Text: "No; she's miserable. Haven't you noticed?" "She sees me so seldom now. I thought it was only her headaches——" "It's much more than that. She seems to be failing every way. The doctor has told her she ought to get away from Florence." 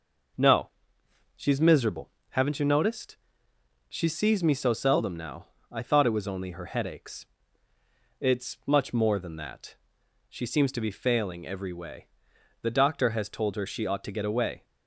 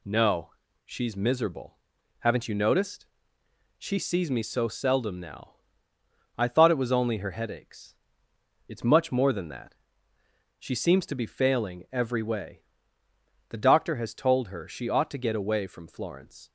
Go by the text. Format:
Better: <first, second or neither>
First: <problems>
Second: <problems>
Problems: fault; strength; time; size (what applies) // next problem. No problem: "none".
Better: second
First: stops before "from Florence"; at 14.6 s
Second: none